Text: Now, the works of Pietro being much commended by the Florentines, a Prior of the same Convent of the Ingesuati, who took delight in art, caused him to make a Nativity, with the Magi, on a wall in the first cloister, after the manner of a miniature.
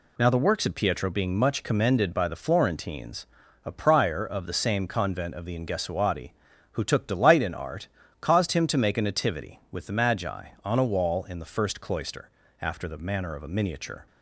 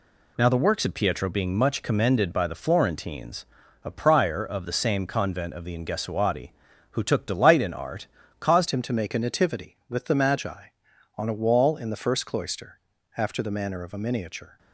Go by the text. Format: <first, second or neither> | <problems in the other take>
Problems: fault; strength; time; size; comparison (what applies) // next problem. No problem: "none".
first | changes voice at "him"; from 8.6 s on; 5.9 s long